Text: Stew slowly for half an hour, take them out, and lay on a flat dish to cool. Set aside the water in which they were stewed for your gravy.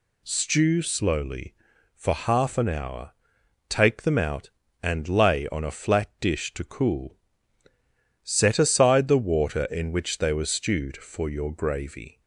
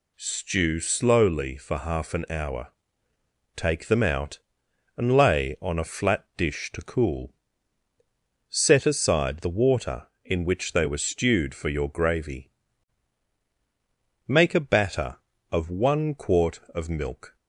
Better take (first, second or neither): first